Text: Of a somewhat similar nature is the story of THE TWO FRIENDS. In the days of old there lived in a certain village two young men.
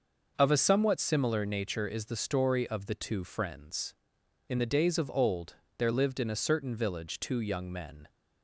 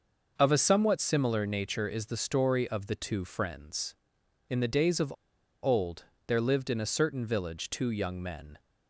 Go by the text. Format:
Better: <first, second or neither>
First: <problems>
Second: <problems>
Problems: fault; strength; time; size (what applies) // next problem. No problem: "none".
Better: first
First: pauses between "old" and "there"; slight; at 5.5 s; 0.24 s long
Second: pauses between "of" and "old"; noticeable; at 5.0 s; 0.53 s long // pauses between "old" and "there"; slight; at 6.0 s; 0.24 s long